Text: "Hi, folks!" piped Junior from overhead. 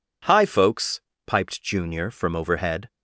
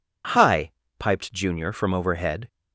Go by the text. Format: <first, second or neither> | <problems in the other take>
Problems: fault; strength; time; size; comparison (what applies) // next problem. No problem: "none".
first | skips "folks"; at 0.8 s